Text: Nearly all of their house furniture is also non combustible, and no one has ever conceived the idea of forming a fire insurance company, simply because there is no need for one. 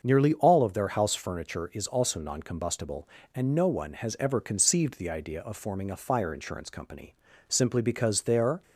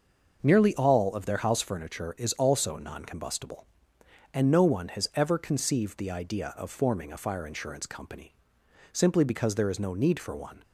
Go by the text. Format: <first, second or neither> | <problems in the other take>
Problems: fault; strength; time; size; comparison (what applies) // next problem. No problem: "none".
second | starts louder than the rest; until 1.0 s; 6.5 dB; noticeable in the second // stops before "is no need for one"; at 8.6 s